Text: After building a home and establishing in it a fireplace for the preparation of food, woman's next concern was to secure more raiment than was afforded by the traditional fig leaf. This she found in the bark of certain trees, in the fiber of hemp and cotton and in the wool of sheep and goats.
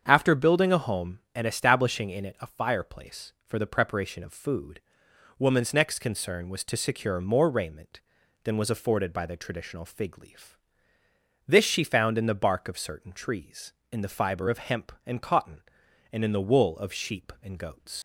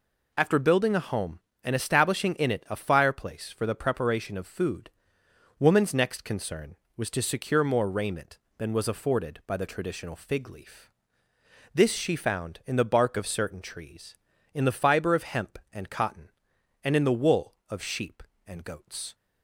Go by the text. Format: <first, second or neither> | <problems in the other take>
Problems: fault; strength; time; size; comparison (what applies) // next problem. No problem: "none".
second | starts louder than the rest; strong; until 1.0 s; 7.5 dB // leaves "goats" unfinished; at 17.9 s; 90 ms